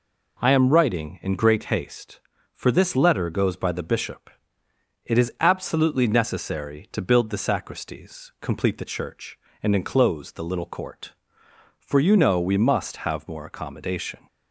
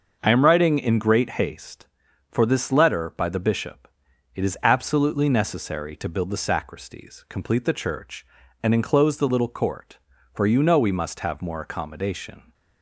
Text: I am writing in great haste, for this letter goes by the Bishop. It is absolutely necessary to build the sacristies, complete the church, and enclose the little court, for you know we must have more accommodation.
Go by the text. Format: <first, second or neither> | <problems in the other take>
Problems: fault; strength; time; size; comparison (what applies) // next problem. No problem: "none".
first | starts louder than the rest; until 1.2 s; 6.5 dB // skips "goes"; at 3.1 s